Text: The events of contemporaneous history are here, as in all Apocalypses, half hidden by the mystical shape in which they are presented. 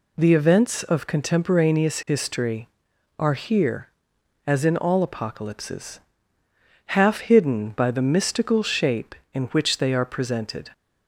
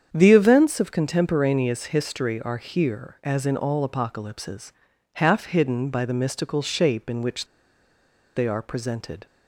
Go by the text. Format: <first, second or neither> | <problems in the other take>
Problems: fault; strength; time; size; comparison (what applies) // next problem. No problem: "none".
first | starts louder than the rest; strong; until 1.1 s; 8 dB // pauses between "which" and "they"; noticeable; at 7.4 s; 0.91 s long